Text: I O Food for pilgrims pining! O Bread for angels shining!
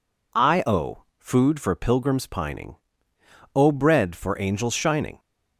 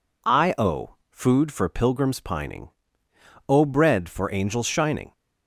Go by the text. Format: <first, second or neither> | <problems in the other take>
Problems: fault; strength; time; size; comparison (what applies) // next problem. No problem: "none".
neither | none